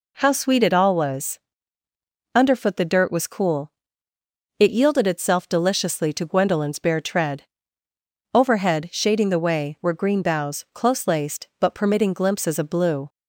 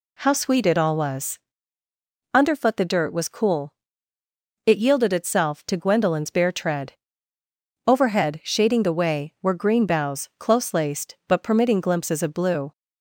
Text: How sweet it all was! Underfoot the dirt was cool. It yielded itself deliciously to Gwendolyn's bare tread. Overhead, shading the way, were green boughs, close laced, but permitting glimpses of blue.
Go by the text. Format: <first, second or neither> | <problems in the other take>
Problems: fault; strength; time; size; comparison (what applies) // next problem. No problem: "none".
first | skips "deliciously"; at 5.6 s